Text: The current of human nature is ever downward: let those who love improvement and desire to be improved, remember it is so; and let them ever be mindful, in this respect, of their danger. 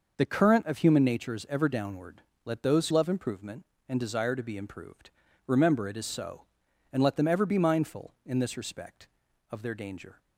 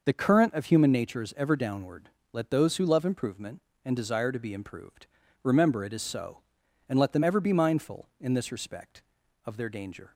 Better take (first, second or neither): second